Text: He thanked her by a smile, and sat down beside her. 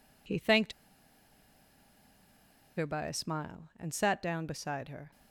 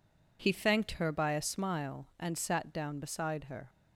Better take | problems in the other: second | pauses between "thanked" and "her"; strong; at 0.7 s; 2.0 s long

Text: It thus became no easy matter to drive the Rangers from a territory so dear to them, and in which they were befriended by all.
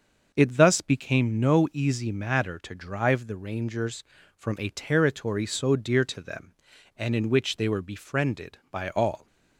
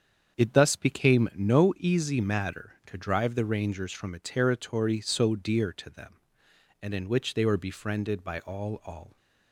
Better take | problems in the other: first | starts louder than the rest; strong; until 1.4 s; 7.5 dB; also in the first // says "all" twice; at 8.8 s

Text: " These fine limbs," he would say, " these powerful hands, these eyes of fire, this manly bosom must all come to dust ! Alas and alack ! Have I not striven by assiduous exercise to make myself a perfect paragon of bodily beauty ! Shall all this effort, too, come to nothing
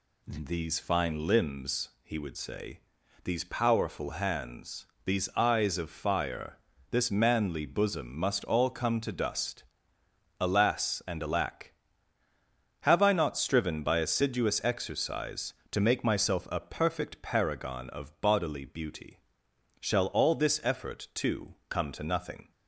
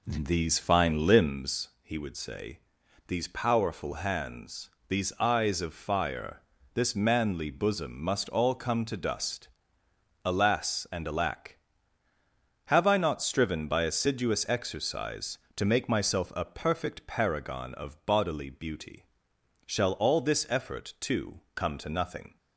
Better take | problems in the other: first | starts louder than the rest; slight; until 1.5 s; 2.5 dB

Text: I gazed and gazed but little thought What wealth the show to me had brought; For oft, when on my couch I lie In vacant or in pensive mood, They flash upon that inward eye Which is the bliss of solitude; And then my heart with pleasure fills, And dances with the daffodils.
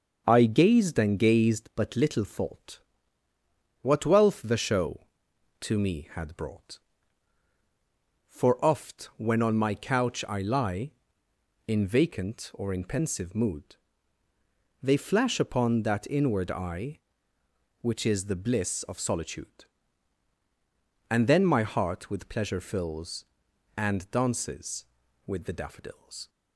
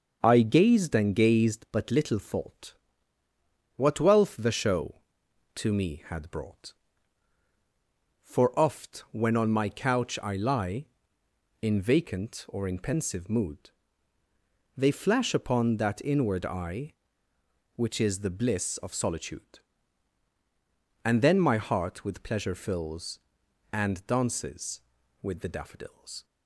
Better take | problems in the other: neither | starts louder than the rest; noticeable; the same in both // pauses between "thought" and "What"; the same in both

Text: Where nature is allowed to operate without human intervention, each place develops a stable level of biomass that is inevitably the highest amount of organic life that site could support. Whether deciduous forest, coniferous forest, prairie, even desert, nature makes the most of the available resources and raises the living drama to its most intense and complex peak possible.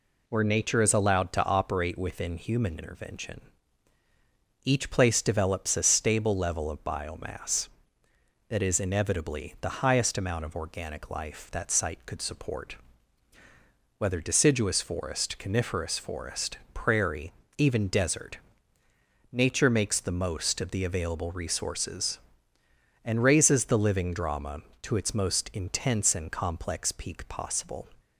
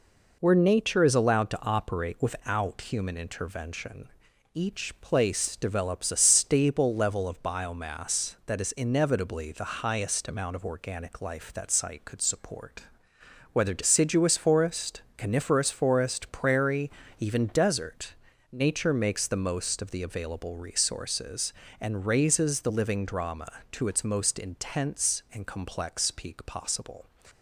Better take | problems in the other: second | says "within" for "without"; at 1.9 s

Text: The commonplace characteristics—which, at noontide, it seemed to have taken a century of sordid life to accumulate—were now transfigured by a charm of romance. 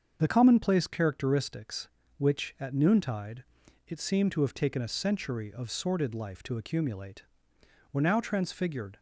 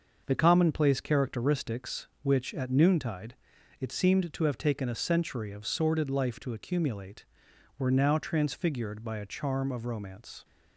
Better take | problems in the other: second | starts louder than the rest; until 1.2 s; 7 dB; also in the second // stops before "by a charm of romance"; at 8.9 s

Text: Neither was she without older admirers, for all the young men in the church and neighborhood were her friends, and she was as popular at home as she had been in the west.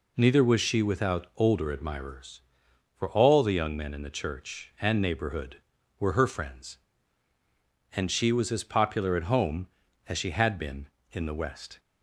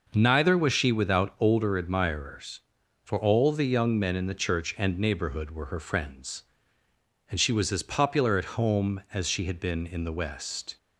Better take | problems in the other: neither | none

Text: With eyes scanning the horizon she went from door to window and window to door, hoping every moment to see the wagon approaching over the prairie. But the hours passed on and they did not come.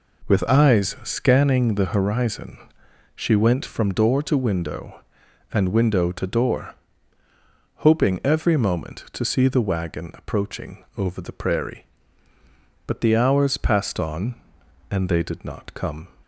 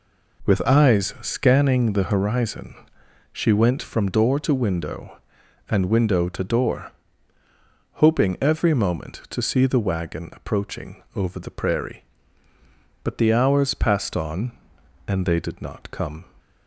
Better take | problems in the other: neither | pauses between "horizon" and "she"; noticeable; the same in both

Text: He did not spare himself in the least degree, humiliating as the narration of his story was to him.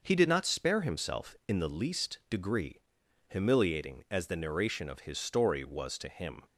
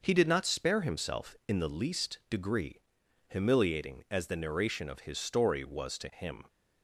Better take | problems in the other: neither | none

